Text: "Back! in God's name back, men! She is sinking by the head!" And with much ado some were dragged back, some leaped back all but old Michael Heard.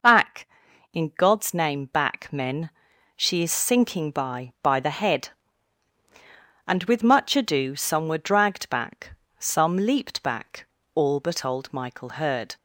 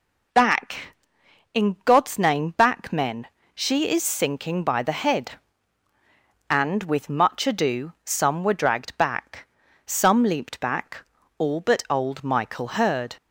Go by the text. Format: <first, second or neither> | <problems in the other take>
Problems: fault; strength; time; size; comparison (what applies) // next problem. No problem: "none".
second | says "by" twice; at 4.6 s // pauses between "back" and "all"; slight; at 10.6 s; 0.28 s long; slight in the second